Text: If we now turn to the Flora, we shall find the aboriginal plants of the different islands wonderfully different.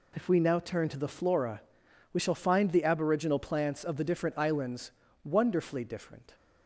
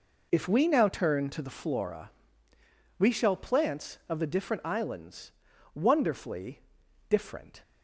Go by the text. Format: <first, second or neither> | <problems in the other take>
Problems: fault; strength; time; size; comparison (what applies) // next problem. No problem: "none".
first | skips "find the aboriginal"; at 3.3 s // pauses between "islands" and "wonderfully"; at 5.3 s; 0.42 s long; slight in the first // pauses between "wonderfully" and "different"; noticeable; at 6.5 s; 0.48 s long